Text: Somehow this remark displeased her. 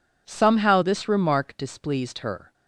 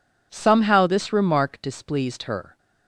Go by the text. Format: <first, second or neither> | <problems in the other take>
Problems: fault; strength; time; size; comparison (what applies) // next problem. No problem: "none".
neither | none